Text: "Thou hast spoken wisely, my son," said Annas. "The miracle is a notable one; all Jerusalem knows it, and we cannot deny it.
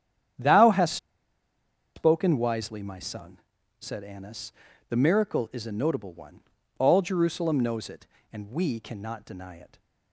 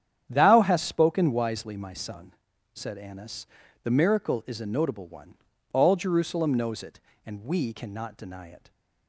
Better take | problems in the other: second | starts louder than the rest; strong; until 2.3 s; 9.5 dB; strong in the second // pauses between "hast" and "spoken"; at 0.9 s; 0.99 s long

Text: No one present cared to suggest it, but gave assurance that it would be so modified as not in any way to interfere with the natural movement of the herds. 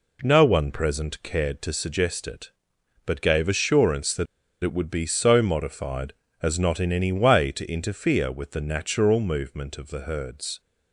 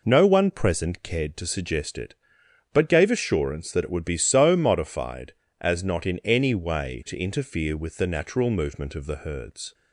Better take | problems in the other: second | pauses between "that" and "it"; at 4.2 s; 0.38 s long

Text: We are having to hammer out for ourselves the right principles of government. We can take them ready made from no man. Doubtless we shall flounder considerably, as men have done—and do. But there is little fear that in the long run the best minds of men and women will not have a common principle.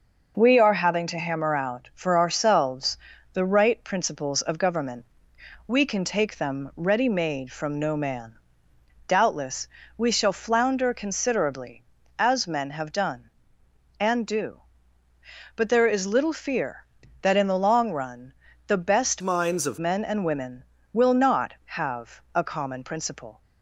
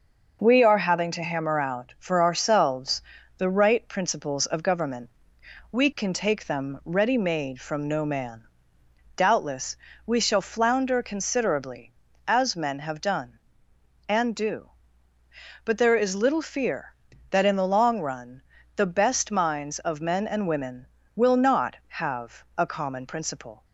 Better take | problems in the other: second | pauses between "ourselves" and "the"; slight; at 2.9 s; 0.34 s long; slight in the second // pauses between "Doubtless" and "we"; slight; at 9.6 s; 0.30 s long; slight in the second // pauses between "run" and "the"; slight; at 18.3 s; 0.34 s long; slight in the second // changes voice from "minds" to "of"; from 19.2 to 19.7 s; 0.5 s long

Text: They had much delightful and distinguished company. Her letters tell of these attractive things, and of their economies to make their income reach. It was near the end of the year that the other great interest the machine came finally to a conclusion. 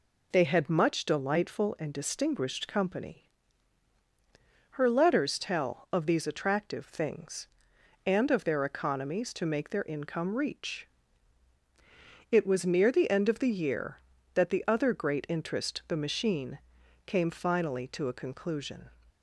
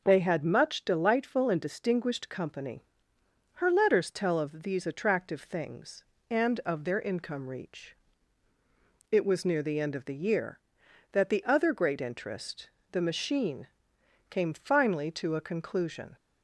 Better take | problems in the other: first | skips "their economies to make"; at 6.8 s // pauses between "interest" and "the"; slight; at 12.6 s; 0.22 s long // pauses between "machine" and "came"; noticeable; at 13.6 s; 0.62 s long; noticeable in the first

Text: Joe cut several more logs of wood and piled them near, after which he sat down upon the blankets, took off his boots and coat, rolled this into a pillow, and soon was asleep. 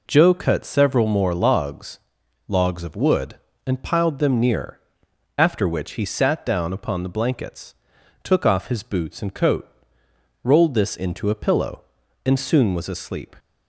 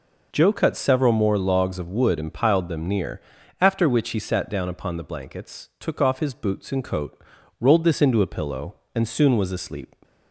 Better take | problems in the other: second | says "logs" twice; at 2.4 s

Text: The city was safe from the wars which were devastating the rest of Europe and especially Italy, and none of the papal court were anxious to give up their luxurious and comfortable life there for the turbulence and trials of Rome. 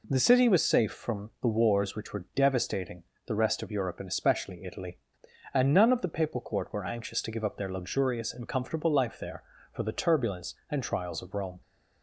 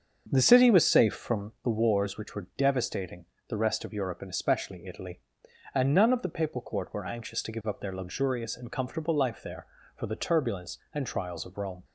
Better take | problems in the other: first | starts louder than the rest; until 1.6 s; 7 dB // pauses between "devastating" and "the"; slight; at 3.2 s; 0.24 s long; slight in the first

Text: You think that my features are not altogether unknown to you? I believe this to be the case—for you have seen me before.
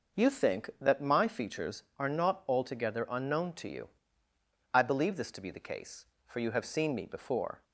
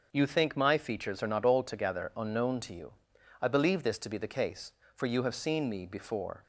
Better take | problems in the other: first | starts louder than the rest; until 1.1 s; 6 dB // skips "that"; at 0.5 s

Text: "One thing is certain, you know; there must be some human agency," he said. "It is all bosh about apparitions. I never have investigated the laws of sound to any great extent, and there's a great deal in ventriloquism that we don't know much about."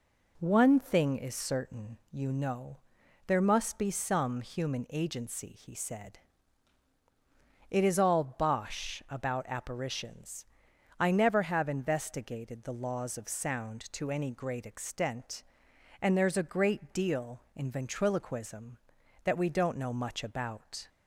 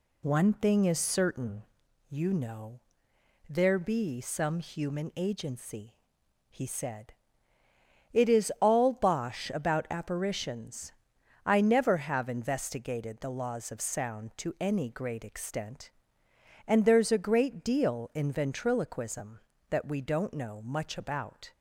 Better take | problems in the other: first | skips "must"; at 3.7 s

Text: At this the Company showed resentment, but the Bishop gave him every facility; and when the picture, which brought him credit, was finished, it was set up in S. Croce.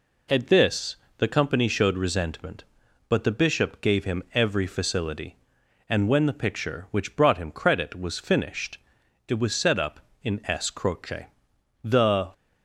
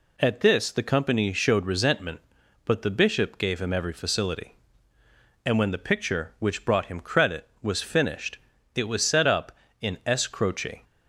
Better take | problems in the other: second | pauses between "this" and "the"; slight; at 0.9 s; 0.22 s long // goes on to say "The"; slight; from 11.8 s on; 0.48 s long

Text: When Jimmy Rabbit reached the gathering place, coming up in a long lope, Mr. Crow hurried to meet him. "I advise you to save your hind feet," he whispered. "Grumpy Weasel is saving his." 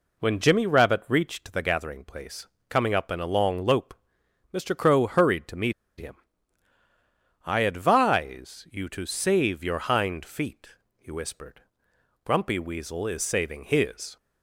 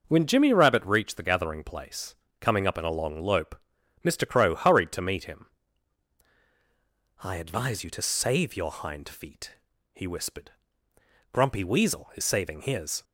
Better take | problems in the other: second | pauses between "meet" and "him"; slight; at 5.7 s; 0.27 s long

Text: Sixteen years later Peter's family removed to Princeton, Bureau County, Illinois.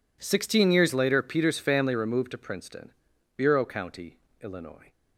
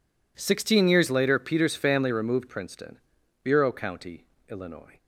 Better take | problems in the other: first | skips "to"; at 2.4 s

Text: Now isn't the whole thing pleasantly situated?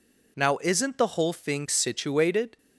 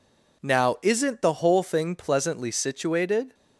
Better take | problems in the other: second | skips "pleasantly"; at 1.6 s

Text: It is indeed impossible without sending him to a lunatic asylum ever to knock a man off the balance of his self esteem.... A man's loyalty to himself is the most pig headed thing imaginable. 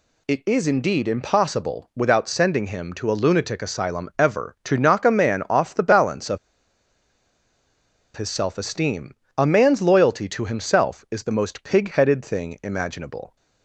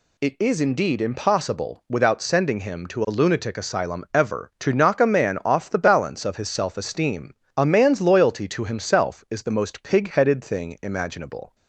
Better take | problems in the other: second | pauses between "of" and "his"; strong; at 6.3 s; 1.7 s long

